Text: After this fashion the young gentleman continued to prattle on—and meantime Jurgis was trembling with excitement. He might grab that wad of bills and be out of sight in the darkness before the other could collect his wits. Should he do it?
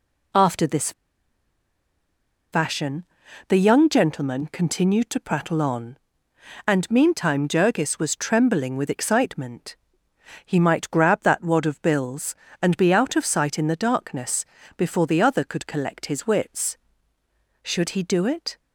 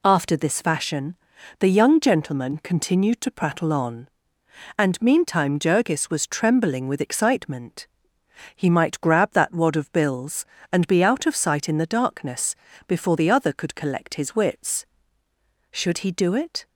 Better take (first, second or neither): second